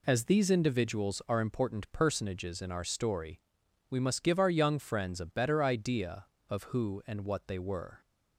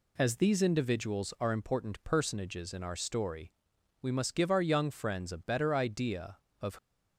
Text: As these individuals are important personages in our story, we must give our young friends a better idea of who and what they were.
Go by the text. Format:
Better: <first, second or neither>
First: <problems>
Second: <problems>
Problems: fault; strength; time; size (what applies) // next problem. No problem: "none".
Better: first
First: none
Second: stops before "who and what they were"; at 6.7 s